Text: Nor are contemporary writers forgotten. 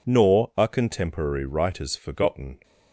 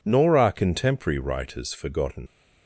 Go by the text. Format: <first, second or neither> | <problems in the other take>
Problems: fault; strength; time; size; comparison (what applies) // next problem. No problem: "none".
first | leaves "forgotten" unfinished; at 2.2 s; 65 ms